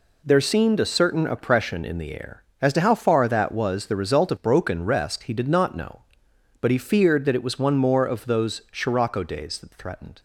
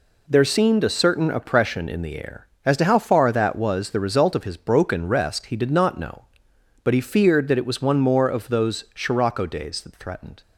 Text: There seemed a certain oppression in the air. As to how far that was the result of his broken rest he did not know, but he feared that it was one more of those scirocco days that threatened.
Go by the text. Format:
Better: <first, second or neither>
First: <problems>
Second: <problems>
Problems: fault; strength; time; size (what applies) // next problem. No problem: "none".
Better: second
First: skips "his"; at 4.3 s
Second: none